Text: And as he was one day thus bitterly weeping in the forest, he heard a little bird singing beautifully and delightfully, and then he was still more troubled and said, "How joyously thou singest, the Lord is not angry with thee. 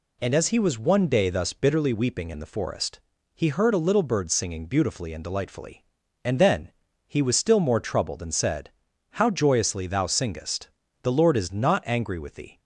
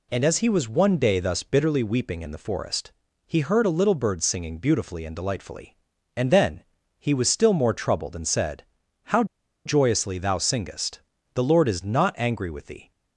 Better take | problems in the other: first | pauses between "then" and "he"; slight; at 6.6 s; 0.36 s long; slight in the first // pauses between "How" and "joyously"; at 9.2 s; 0.41 s long

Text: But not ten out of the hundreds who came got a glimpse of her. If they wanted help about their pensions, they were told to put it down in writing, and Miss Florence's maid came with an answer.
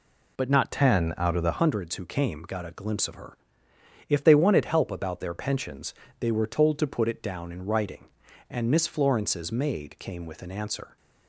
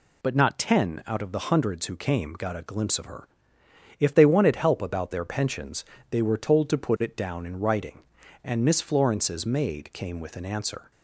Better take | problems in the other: second | changes voice from "ten" to "the"; from 0.7 to 1.5 s; 0.8 s long

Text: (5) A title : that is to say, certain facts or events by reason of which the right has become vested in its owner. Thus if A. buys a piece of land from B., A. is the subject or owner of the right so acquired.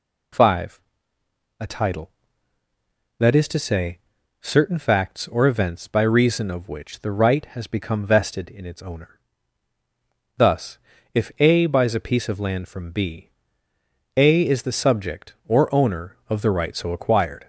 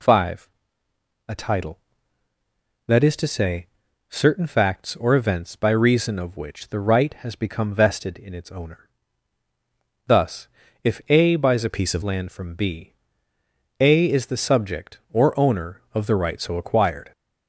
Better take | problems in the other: first | pauses between "Thus" and "if"; slight; at 10.4 s; 0.34 s long; slight in the first // changes voice from "piece" to "of"; from 11.7 to 12.0 s; 0.3 s long

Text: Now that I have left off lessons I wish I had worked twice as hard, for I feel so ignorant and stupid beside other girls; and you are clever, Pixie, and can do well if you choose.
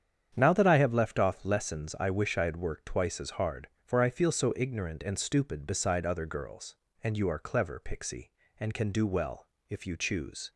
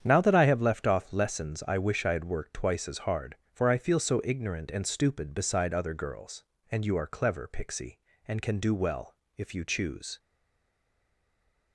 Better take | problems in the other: first | starts louder than the rest; strong; until 1.0 s; 8.5 dB; strong in the first // pauses between "well" and "if"; slight; at 9.1 s; 0.24 s long; slight in the first // stays silent after the last word; noticeable; from 10.1 s on; 1.6 s long

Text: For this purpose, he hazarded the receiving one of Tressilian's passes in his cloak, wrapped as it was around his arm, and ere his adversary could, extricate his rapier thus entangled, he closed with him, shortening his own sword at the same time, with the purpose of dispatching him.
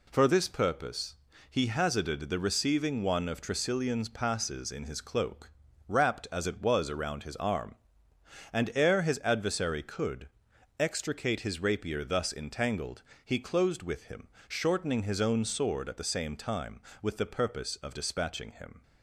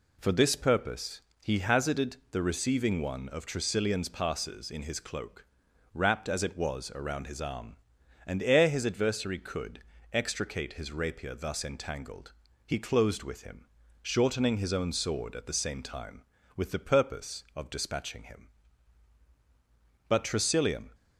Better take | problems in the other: first | goes on to say "But Tressilian"; noticeable; from 20.0 s on; 0.80 s long

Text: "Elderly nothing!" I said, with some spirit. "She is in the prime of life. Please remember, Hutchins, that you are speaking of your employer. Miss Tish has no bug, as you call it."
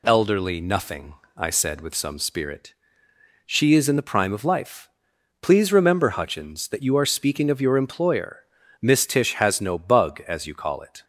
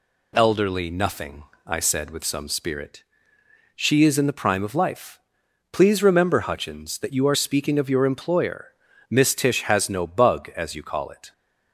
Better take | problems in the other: neither | none

